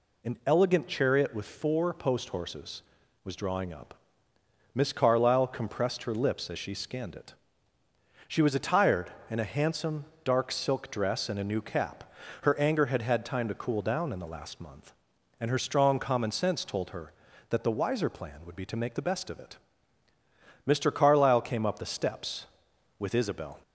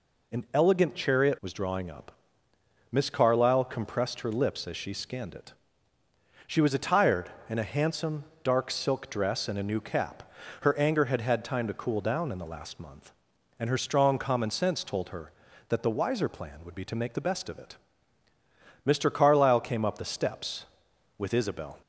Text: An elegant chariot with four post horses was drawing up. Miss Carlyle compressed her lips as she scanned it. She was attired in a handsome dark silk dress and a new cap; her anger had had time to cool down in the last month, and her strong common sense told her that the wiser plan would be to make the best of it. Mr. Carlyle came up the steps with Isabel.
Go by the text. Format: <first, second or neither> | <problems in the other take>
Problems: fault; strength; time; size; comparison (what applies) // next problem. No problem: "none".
first | skips "with four post horses"; at 1.4 s // pauses between "handsome" and "dark"; slight; at 8.2 s; 0.18 s long; slight in the first